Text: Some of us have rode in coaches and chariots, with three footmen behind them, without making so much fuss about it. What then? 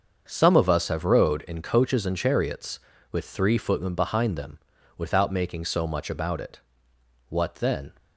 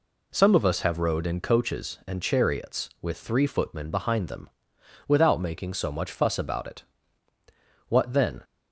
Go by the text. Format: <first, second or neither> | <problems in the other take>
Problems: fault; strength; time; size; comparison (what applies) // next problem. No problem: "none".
second | starts louder than the rest; until 1.2 s; 6.5 dB // skips "fuss"; at 6.1 s